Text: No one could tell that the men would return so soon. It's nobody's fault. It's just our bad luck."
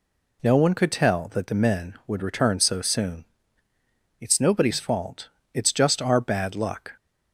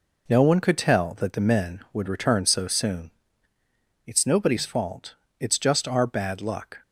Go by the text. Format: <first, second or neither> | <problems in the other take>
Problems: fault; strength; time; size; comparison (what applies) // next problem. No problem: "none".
first | gets quieter; strong; throughout; 7.5 dB